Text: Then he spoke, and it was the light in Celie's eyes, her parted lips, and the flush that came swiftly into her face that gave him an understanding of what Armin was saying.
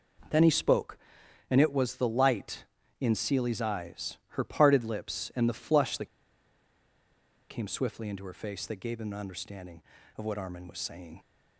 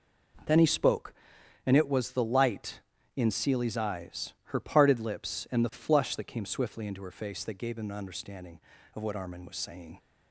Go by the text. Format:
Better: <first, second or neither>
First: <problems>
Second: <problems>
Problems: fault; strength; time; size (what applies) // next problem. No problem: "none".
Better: second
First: pauses between "that" and "came"; strong; at 6.0 s; 1.4 s long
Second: none